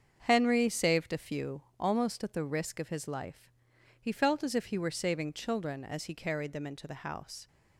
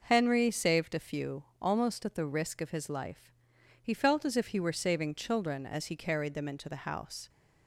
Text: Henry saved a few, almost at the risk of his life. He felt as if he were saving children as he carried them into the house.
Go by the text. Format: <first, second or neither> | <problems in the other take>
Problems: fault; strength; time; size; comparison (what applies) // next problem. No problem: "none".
second | gets quieter; strong; throughout; 7.5 dB